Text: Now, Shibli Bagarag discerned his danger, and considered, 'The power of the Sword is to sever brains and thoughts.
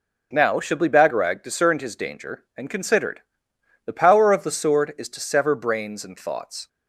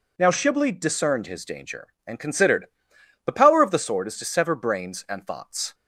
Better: first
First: none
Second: skips "Bagarag"; at 0.7 s

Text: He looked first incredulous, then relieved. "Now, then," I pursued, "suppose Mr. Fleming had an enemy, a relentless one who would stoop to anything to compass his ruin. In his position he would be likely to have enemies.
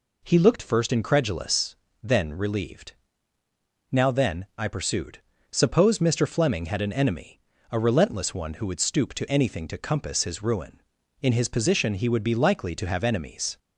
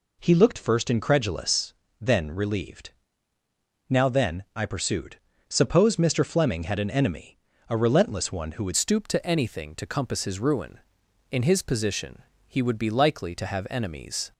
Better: first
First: none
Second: changes voice at "stoop"; from 8.7 s on; 5.6 s long // pauses between "position" and "he"; slight; at 12.2 s; 0.26 s long

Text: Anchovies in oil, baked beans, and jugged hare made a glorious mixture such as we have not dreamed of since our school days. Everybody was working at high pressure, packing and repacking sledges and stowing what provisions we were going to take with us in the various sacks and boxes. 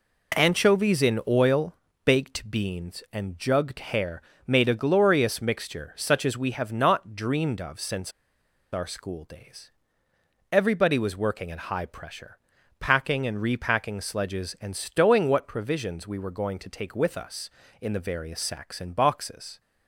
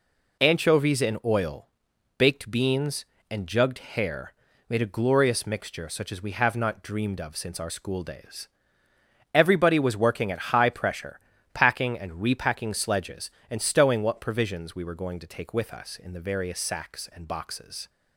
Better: second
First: pauses between "hare" and "made"; slight; at 4.2 s; 0.24 s long // pauses between "since" and "our"; noticeable; at 8.1 s; 0.61 s long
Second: pauses between "hare" and "made"; slight; at 4.3 s; 0.34 s long

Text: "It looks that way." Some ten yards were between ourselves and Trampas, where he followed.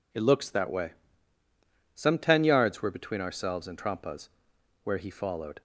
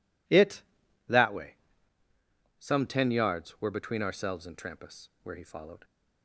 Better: first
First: none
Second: skips "looks"; at 0.8 s

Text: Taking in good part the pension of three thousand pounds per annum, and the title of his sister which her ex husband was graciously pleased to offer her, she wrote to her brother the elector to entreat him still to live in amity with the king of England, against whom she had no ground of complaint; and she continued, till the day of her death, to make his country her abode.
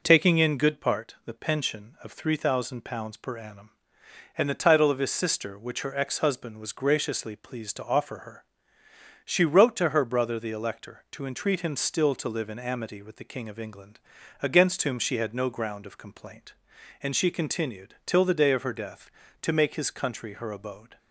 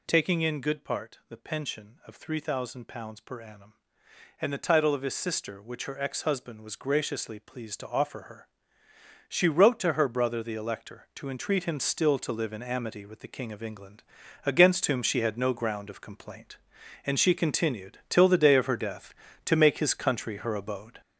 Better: first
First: none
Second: gets louder; throughout; 6 dB

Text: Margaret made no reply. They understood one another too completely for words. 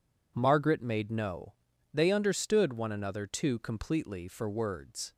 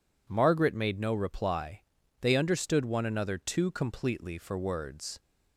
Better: second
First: skips "reply"; at 1.7 s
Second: none

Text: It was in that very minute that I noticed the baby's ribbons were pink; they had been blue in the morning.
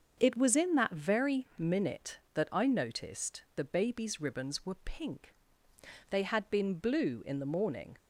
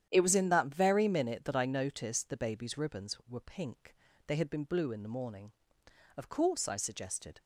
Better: first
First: starts louder than the rest; until 1.1 s; 6.5 dB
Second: starts louder than the rest; strong; until 1.1 s; 10 dB // goes on to say "Of course I suggested"; noticeable; from 6.1 s on; 1.2 s long

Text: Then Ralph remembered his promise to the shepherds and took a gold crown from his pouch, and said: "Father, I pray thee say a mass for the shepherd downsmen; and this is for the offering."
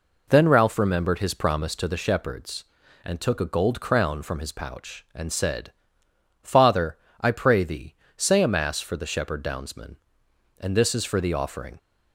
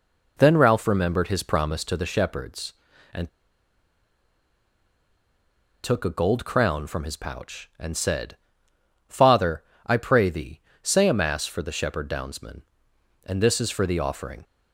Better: first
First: pauses between "thee" and "say"; slight; at 7.9 s; 0.24 s long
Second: pauses between "and" and "took"; strong; at 3.2 s; 2.5 s long // pauses between "thee" and "say"; slight; at 10.5 s; 0.24 s long

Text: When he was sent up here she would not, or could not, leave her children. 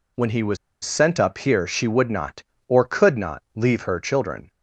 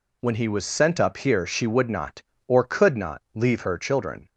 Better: second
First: pauses between "was" and "sent"; slight; at 0.5 s; 0.26 s long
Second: none

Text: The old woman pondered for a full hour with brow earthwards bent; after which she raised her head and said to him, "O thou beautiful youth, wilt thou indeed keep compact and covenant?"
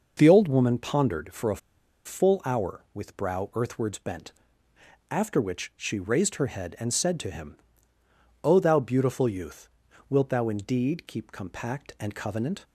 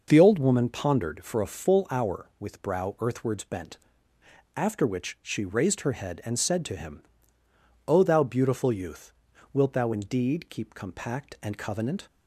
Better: second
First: pauses between "a" and "full"; noticeable; at 1.5 s; 0.47 s long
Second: none

